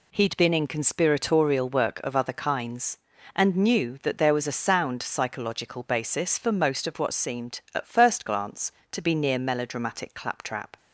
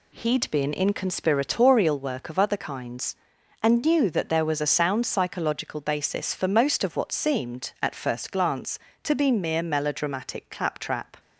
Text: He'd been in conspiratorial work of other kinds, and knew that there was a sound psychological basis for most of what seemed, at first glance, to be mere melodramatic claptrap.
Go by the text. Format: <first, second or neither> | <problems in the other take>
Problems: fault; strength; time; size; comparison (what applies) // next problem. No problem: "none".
second | says "near" for "mere"; at 9.1 s